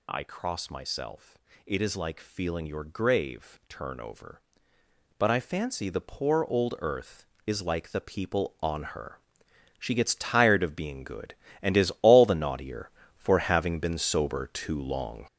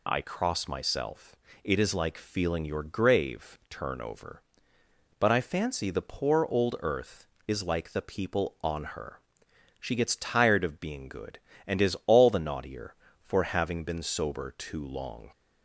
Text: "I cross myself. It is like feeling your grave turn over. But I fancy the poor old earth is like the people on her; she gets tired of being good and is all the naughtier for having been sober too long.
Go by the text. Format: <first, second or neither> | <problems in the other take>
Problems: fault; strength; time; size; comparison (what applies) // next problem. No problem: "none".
second | gets louder; strong; throughout; 7.5 dB